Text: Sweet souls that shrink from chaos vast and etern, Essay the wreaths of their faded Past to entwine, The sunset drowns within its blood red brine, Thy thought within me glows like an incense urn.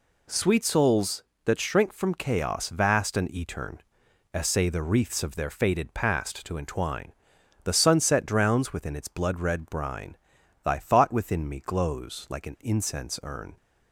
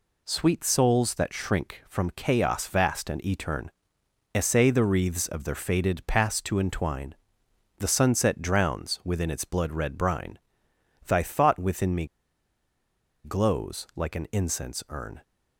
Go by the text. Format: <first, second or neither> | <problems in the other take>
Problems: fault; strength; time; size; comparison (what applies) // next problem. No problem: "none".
first | pauses between "me" and "glows"; at 12.0 s; 1.1 s long